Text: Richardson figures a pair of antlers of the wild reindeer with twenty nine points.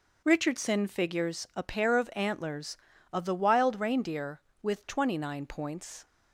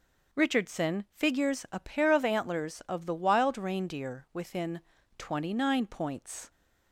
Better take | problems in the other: first | says "within" for "with"; at 4.3 s

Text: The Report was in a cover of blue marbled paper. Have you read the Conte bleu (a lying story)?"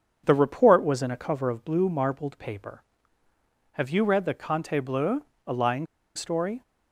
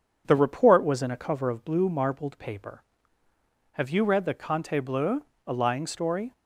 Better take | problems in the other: second | pauses between "lying" and "story"; slight; at 5.8 s; 0.30 s long

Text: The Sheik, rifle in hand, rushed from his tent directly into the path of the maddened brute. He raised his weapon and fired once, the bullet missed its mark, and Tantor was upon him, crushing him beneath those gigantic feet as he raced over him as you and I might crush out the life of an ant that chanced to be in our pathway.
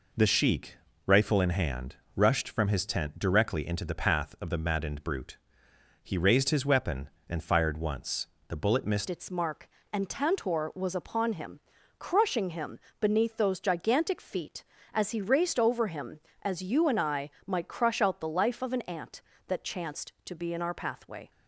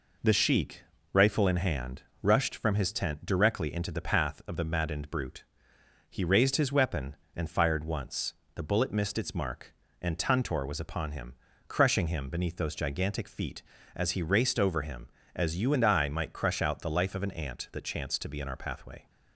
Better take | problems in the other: second | changes voice at "its"; from 9.0 s on; 12.3 s long // pauses between "him" and "beneath"; slight; at 12.7 s; 0.22 s long // pauses between "I" and "might"; slight; at 17.3 s; 0.16 s long

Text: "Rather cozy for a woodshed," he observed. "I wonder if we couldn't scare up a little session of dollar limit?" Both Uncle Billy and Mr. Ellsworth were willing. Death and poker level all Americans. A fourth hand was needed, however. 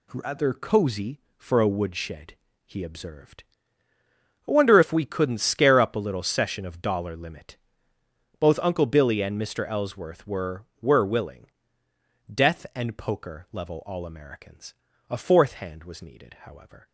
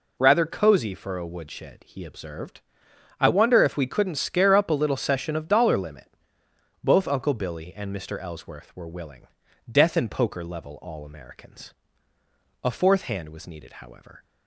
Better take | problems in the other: second | says "were" twice; at 10.8 s

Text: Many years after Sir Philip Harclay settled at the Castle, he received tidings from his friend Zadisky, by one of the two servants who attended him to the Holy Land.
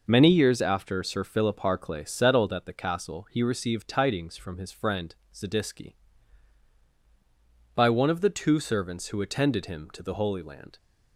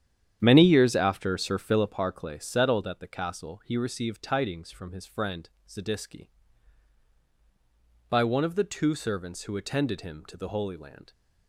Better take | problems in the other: first | starts louder than the rest; strong; until 1.9 s; 9.5 dB // pauses between "friend" and "Zadisky"; slight; at 5.4 s; 0.18 s long; slight in the first

